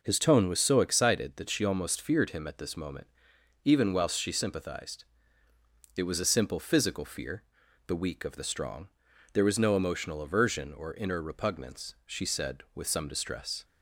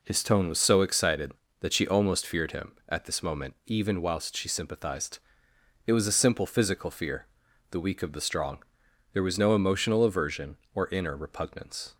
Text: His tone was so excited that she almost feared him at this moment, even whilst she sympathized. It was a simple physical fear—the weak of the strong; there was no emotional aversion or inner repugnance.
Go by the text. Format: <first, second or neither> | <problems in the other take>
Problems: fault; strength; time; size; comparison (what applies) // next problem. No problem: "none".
second | goes on to say "She said with some distress"; from 12.0 s on; 1.5 s long